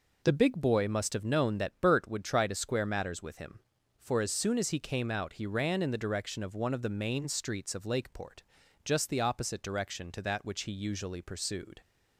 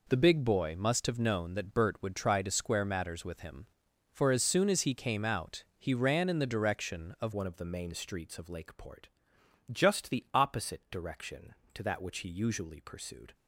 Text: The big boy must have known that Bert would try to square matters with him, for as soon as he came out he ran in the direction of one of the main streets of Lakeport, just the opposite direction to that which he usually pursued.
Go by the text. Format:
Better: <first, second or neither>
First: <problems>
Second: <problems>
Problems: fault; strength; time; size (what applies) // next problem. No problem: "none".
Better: first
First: none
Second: changes voice at "one"; from 7.3 s on; 6.0 s long